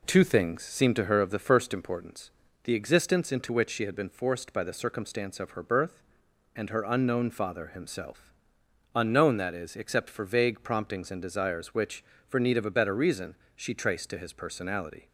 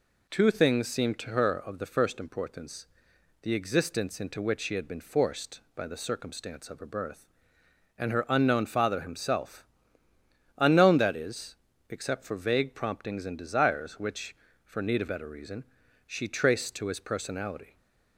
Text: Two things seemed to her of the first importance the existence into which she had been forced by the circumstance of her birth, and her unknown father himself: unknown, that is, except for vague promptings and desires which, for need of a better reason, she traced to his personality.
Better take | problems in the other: first | pauses between "importance" and "the"; noticeable; at 2.8 s; 0.58 s long; slight in the first // skips "a"; at 15.0 s

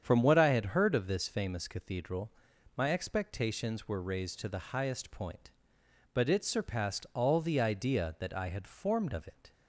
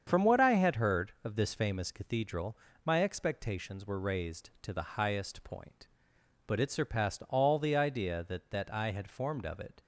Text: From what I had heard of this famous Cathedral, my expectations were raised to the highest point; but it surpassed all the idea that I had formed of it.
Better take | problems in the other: first | starts louder than the rest; strong; until 1.0 s; 7.5 dB; strong in the first // says "that" twice; at 8.4 s

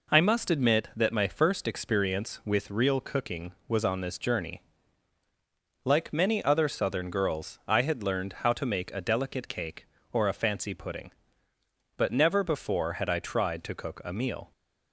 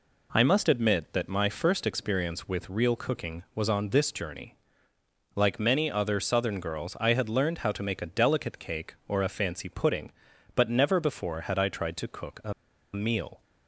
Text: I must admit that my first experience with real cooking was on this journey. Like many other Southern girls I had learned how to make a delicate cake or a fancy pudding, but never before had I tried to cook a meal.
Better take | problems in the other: first | pauses between "a" and "meal"; at 12.5 s; 0.40 s long

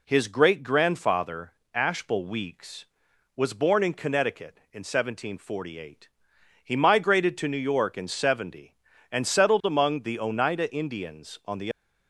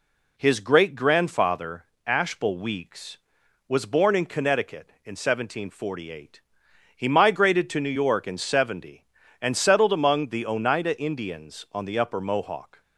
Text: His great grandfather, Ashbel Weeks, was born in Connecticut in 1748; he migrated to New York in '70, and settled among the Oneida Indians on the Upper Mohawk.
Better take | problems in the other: second | stops before "Upper Mohawk"; at 11.7 s

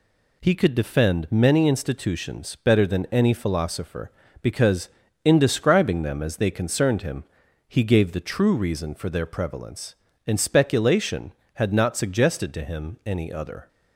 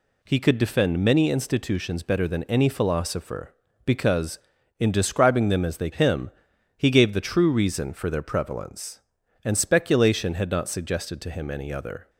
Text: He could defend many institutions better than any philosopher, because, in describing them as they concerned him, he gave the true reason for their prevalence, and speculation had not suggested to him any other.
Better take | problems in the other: first | skips "concerned"; at 5.9 s

